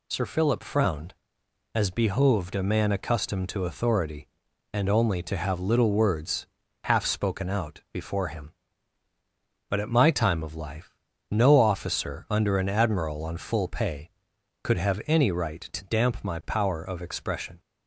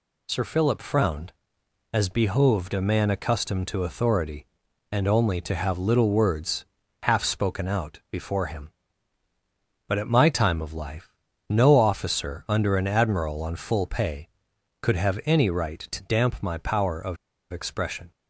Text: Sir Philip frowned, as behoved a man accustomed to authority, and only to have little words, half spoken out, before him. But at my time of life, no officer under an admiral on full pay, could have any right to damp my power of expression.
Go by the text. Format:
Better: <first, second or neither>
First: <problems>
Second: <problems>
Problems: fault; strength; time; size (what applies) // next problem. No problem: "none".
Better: first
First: none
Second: pauses between "of" and "expression"; at 17.1 s; 0.36 s long